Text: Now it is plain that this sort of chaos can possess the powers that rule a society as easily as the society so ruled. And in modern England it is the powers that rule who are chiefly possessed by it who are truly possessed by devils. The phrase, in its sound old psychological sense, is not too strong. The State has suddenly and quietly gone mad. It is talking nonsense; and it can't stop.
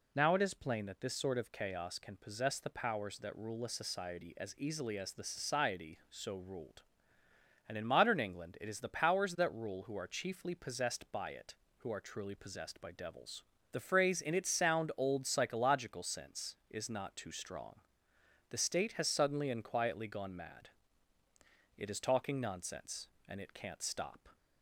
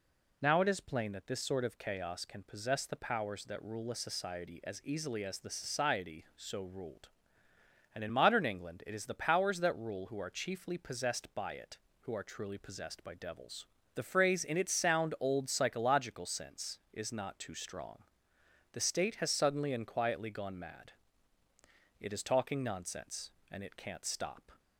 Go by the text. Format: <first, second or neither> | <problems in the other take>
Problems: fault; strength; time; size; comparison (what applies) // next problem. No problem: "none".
neither | none